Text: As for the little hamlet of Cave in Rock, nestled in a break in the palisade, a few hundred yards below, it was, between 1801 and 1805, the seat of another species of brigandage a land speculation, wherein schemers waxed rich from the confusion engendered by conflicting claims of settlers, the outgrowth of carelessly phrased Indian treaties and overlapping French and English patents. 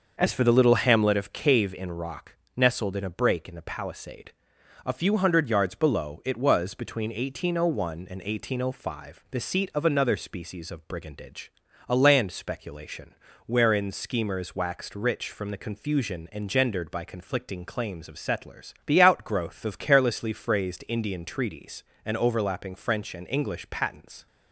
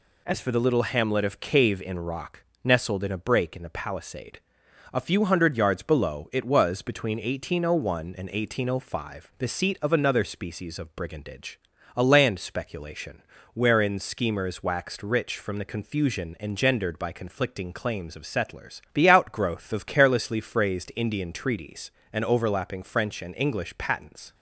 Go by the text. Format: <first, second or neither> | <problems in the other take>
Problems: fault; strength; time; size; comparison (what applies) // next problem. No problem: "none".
second | starts louder than the rest; noticeable; until 1.2 s; 6 dB // pauses between "brigandage" and "a"; at 11.5 s; 0.38 s long; also in the second